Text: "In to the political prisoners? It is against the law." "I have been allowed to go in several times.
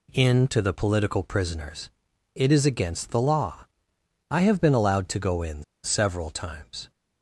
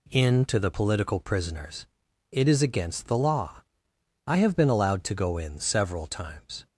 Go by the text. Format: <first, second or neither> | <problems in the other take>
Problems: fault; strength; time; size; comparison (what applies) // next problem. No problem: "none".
second | pauses between "in" and "several"; slight; at 5.6 s; 0.20 s long